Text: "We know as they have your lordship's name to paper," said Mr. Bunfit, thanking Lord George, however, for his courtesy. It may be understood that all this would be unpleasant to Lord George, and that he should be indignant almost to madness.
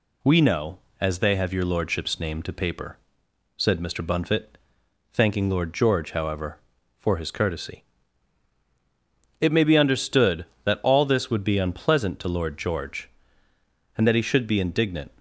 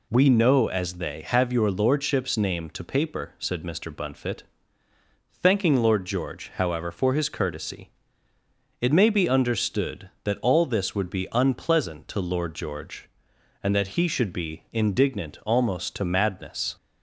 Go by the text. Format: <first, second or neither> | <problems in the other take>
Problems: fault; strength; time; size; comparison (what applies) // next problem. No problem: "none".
second | stops before "almost to madness"; at 15.1 s